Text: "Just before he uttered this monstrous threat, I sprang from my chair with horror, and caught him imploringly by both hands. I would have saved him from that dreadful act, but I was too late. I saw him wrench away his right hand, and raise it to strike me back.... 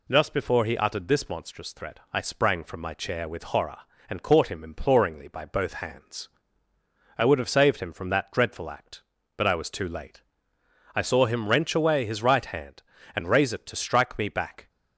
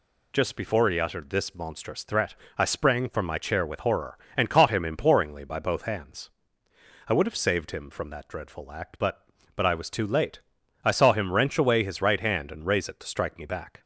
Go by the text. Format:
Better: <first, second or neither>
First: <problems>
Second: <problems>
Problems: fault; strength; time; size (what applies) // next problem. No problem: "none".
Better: first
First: none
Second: says "but" twice; at 9.5 s